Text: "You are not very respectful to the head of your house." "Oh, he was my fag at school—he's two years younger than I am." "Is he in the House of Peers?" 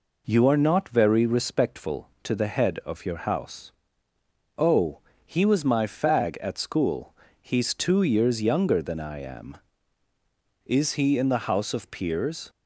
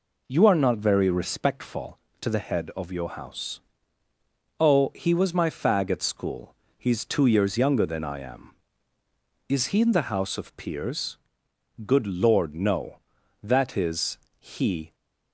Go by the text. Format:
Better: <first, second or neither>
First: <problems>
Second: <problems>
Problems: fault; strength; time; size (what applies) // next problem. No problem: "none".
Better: first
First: none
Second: goes on to say "Good Lord no That is he"; strong; from 11.8 s on; 3.1 s long